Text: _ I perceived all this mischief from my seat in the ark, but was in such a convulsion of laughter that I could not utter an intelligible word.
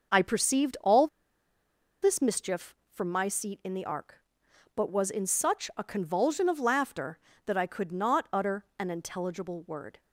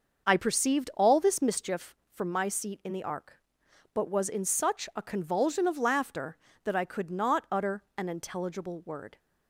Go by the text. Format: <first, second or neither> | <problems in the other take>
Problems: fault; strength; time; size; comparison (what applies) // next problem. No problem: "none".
second | starts louder than the rest; until 2.1 s; 6 dB; noticeable in the second // pauses between "all" and "this"; noticeable; at 1.0 s; 0.95 s long